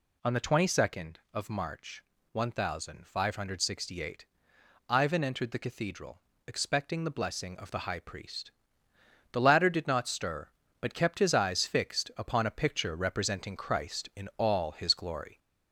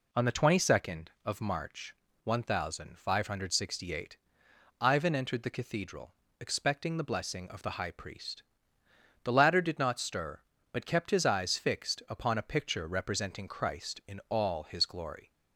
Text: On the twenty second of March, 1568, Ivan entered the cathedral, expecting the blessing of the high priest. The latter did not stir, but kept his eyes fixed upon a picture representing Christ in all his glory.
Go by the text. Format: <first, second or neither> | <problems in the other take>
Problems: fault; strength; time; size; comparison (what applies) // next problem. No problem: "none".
second | gets louder; slight; throughout; 2.5 dB